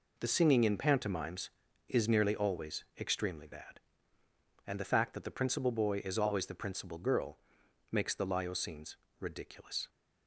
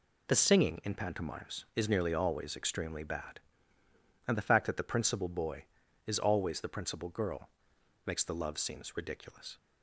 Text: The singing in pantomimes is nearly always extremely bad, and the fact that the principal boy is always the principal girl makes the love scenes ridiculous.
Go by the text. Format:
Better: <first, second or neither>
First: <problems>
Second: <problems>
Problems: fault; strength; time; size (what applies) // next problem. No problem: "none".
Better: second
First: pauses between "girl" and "makes"; noticeable; at 7.3 s; 0.54 s long // says "lyo" for "love"; at 8.2 s // pauses between "scenes" and "ridiculous"; slight; at 8.9 s; 0.22 s long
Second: pauses between "girl" and "makes"; noticeable; at 7.4 s; 0.56 s long